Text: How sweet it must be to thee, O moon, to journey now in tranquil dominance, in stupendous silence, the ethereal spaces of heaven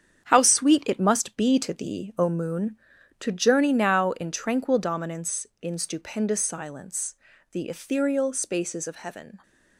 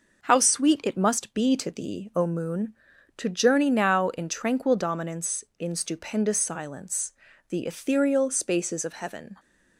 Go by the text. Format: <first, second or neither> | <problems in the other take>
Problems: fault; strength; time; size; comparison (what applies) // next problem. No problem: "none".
second | gets quieter; strong; throughout; 7.5 dB